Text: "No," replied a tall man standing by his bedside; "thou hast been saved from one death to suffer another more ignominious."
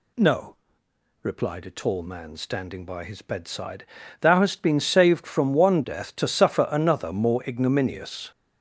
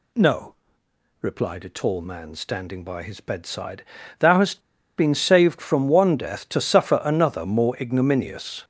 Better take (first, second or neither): first